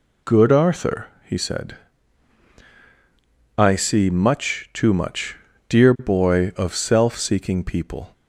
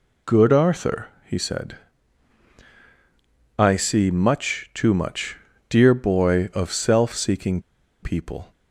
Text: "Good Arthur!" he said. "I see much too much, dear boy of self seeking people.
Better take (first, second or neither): first